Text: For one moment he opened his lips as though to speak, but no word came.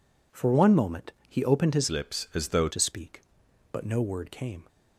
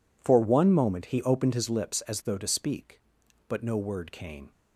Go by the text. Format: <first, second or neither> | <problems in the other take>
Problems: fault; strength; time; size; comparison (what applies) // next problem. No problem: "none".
second | pauses between "moment" and "he"; slight; at 1.1 s; 0.16 s long // changes voice from "lips" to "though"; from 1.8 to 2.6 s; 0.8 s long